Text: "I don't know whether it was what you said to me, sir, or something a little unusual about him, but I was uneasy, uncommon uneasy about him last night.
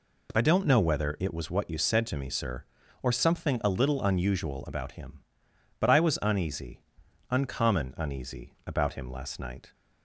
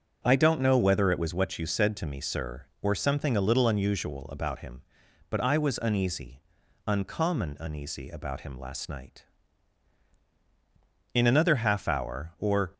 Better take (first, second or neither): first